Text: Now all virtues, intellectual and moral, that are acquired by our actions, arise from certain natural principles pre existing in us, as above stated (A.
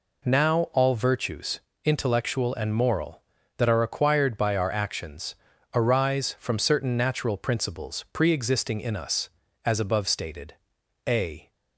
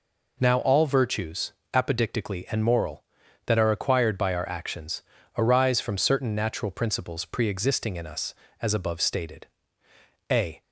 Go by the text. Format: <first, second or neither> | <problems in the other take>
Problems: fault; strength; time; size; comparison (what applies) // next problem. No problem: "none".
first | says "apodictically" for "intellectual"; at 1.7 s